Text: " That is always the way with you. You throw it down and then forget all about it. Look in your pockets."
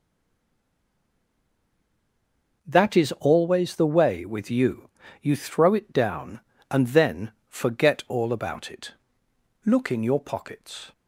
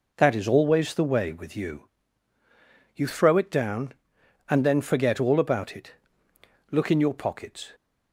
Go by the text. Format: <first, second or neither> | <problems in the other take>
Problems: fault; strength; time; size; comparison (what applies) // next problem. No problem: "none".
second | stays silent before the first word; strong; until 2.6 s; 2.6 s long // pauses between "then" and "forget"; slight; at 7.3 s; 0.16 s long